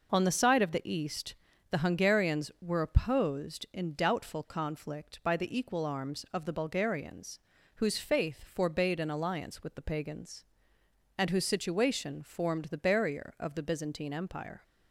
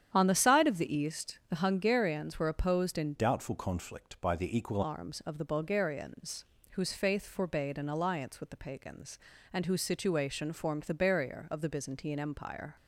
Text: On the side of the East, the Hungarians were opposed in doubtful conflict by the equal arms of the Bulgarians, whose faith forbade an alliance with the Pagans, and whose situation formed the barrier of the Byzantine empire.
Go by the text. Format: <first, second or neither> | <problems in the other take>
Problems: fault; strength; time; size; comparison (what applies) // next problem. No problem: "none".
first | starts louder than the rest; strong; until 1.1 s; 9 dB // changes voice from "doubtful" to "equal"; from 3.1 to 4.8 s; 1.7 s long